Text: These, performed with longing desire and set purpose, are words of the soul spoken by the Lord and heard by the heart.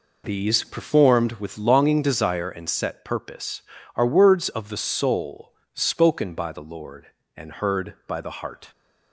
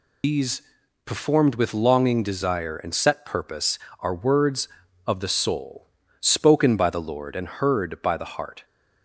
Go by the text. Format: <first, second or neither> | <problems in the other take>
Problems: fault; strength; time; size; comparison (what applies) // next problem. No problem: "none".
first | loses the start of "These"; at 0.2 s; 120 ms // pauses between "soul" and "spoken"; slight; at 5.8 s; 0.34 s long; slight in the first